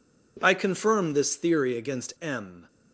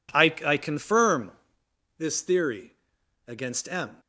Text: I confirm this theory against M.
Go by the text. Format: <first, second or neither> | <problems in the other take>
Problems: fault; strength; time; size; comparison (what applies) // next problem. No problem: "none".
first | says "I" twice; at 0.4 s // pauses between "confirm" and "this"; noticeable; at 1.3 s; 0.66 s long // pauses between "theory" and "against"; noticeable; at 2.7 s; 0.52 s long